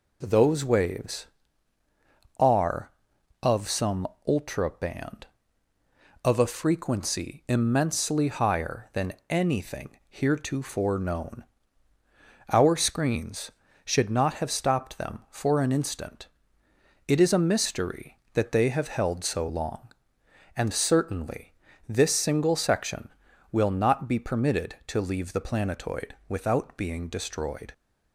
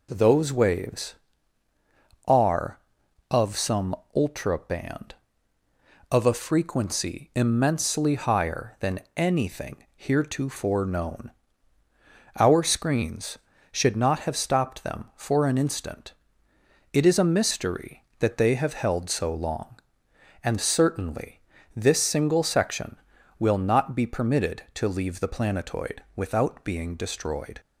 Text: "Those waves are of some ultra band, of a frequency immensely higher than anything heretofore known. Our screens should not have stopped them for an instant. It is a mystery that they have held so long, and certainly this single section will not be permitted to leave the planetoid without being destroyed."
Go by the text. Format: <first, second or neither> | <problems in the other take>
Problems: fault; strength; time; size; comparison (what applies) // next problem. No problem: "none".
neither | pauses between "some" and "ultra"; slight; the same in both // pauses between "than" and "anything"; slight; the same in both // pauses between "certainly" and "this"; slight; the same in both